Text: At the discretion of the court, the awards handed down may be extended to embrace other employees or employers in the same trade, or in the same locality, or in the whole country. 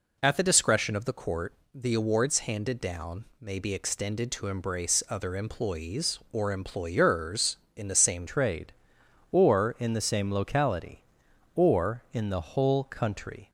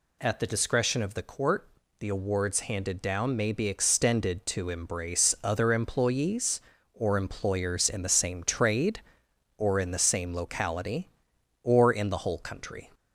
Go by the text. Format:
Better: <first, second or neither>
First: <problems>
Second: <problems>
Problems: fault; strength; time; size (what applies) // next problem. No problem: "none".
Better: second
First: changes voice at "trade"; from 8.2 s on; 5.2 s long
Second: none